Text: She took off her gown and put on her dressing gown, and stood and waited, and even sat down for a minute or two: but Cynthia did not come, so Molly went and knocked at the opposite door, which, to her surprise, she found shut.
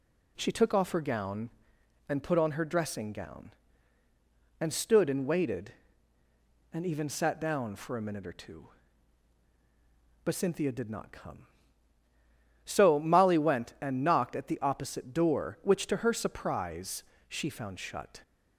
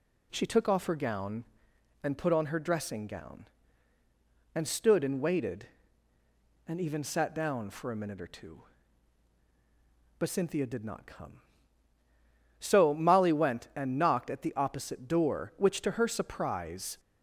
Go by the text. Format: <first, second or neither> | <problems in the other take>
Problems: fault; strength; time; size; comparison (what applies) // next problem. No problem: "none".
first | stops before "she found shut"; at 16.9 s